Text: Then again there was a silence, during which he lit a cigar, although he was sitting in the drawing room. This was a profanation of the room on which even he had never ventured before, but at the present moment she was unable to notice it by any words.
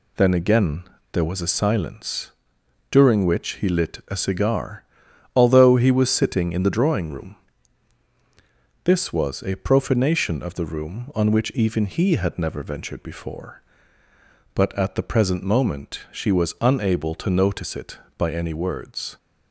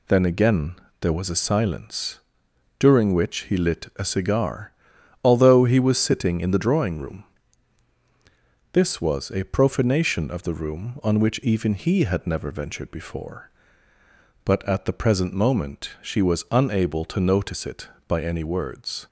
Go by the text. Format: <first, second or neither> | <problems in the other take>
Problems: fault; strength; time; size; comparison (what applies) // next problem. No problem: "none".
neither | pauses between "again" and "there"; slight; the same in both